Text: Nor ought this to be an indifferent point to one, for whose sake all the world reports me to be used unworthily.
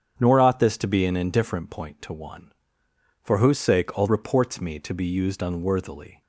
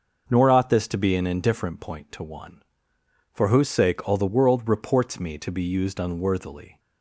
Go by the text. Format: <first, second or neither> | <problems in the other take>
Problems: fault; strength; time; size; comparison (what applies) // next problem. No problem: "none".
second | starts louder than the rest; strong; until 1.1 s; 7.5 dB // skips "the world"; at 4.0 s